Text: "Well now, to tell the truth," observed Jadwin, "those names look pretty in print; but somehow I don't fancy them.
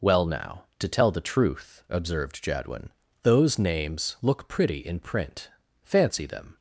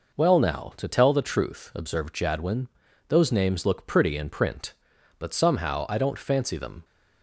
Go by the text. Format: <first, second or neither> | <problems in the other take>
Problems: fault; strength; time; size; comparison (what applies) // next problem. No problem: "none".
second | skips "but somehow I don't"; at 5.6 s